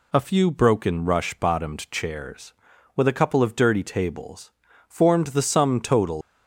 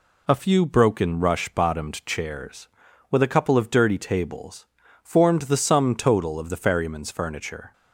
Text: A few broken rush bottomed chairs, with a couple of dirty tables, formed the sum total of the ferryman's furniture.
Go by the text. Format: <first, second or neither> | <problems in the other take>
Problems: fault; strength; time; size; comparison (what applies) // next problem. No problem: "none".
second | stops before "of the ferryman's furniture"; at 6.2 s